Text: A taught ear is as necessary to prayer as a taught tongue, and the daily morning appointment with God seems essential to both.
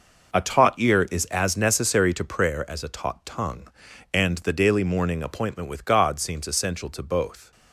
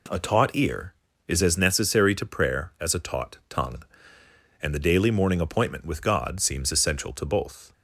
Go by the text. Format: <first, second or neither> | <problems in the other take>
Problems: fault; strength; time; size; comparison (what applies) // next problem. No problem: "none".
second | gets quieter; strong; throughout; 9.5 dB